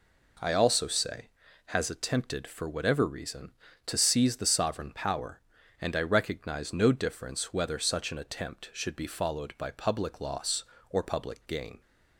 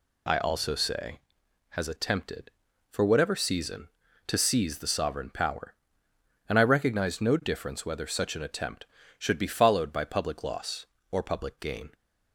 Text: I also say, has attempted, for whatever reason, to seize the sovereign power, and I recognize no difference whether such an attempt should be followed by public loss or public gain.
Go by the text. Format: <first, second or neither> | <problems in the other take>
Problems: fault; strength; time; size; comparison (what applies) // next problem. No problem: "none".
first | says "season" for "reason"; at 3.3 s